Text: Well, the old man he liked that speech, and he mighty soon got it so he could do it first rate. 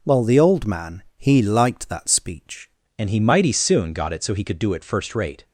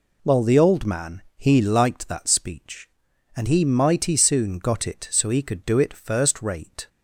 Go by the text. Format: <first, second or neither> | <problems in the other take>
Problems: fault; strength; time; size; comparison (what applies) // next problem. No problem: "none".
second | pauses between "man" and "he"; slight; at 1.0 s; 0.16 s long; slight in the second // changes voice at "and"; from 2.9 s on; 2.5 s long